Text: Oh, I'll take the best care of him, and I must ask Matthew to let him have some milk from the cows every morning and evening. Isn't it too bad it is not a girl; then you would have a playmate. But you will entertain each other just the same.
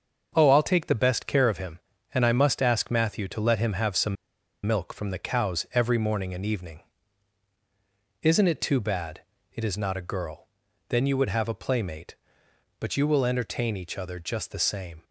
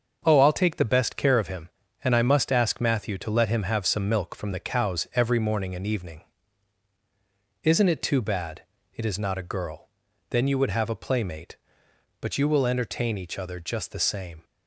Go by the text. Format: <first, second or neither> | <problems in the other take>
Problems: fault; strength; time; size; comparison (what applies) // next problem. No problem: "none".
second | starts louder than the rest; until 1.3 s; 6.5 dB; also in the second // pauses between "some" and "milk"; noticeable; at 4.1 s; 0.50 s long // pauses between "bad" and "it"; slight; at 9.1 s; 0.34 s long; slight in the second